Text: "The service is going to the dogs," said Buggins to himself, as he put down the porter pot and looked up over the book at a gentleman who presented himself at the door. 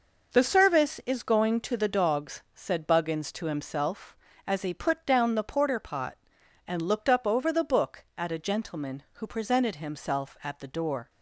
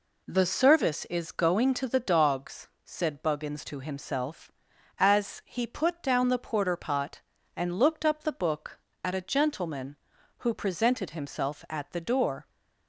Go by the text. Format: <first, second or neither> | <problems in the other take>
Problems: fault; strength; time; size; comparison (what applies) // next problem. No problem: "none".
first | skips "over"; at 8.2 s